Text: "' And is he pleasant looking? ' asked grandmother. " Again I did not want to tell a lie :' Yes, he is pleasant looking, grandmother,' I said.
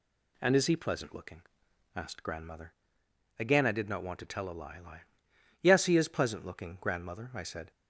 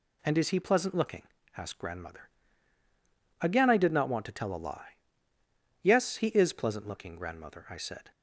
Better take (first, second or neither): second